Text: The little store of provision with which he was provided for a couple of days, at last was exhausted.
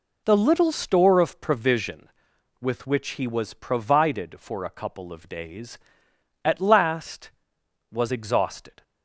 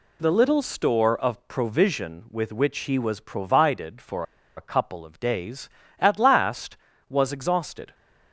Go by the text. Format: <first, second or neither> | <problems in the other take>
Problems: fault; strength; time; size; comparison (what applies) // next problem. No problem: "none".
first | pauses between "for" and "a"; slight; at 4.2 s; 0.34 s long